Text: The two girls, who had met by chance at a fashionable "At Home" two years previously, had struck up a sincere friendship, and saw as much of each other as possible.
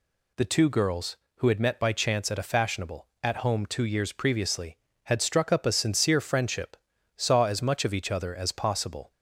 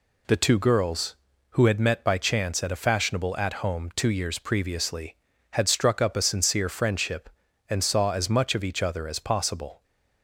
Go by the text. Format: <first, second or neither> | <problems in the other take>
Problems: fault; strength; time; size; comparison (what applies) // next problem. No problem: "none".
second | skips "and"; at 6.9 s